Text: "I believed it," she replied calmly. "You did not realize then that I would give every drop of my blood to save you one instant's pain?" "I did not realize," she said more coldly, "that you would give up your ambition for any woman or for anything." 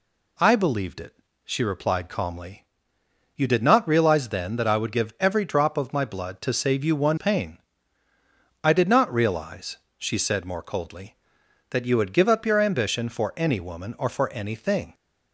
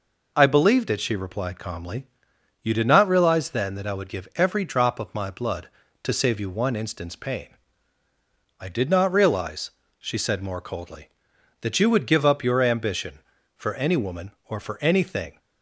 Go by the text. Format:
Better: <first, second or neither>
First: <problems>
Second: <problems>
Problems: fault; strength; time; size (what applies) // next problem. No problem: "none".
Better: second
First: skips "instant's"; at 7.1 s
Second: none